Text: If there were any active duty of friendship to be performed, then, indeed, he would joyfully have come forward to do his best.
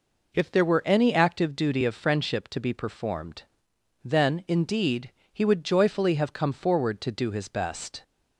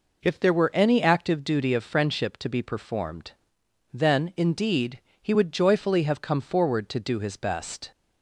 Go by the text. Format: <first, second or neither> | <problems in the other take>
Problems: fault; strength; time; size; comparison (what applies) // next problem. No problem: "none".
neither | none